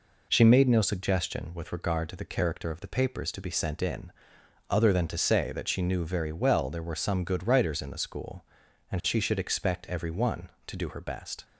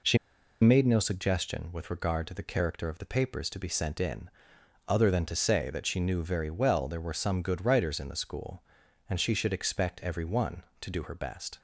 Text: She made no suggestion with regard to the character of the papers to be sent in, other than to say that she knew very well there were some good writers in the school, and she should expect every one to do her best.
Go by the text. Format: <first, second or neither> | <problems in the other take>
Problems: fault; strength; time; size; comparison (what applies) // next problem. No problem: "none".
first | pauses between "She" and "made"; at 0.1 s; 0.45 s long